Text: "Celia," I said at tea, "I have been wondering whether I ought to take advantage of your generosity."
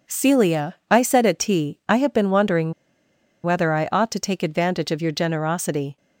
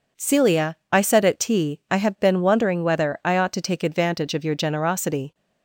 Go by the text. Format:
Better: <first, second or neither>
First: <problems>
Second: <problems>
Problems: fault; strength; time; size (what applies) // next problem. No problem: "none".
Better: second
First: pauses between "wondering" and "whether"; noticeable; at 2.7 s; 0.71 s long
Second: none